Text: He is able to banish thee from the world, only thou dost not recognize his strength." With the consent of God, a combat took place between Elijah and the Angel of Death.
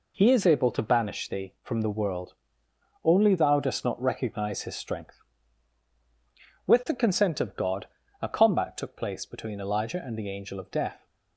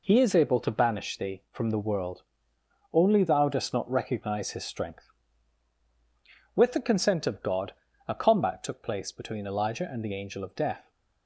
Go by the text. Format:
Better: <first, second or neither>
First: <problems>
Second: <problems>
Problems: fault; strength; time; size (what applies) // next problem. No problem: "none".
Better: neither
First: none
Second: none